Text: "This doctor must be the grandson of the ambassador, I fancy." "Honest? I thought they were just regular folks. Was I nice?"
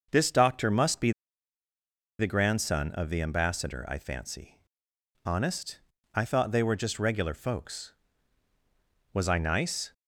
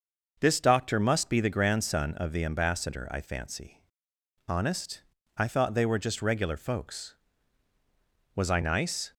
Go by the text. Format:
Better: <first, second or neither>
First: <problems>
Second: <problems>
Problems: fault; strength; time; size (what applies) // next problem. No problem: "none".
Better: second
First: pauses between "be" and "the"; at 1.1 s; 1.0 s long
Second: none